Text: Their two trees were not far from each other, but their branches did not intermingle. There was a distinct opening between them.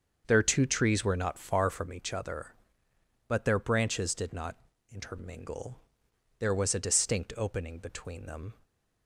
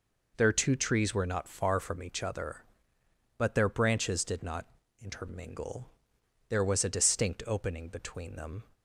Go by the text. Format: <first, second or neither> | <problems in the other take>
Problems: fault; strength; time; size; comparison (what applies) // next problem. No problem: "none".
second | starts louder than the rest; until 1.9 s; 6.5 dB // pauses between "not" and "intermingle"; slight; at 4.5 s; 0.36 s long; slight in the second // stays silent after the last word; slight; from 8.5 s on; 0.5 s long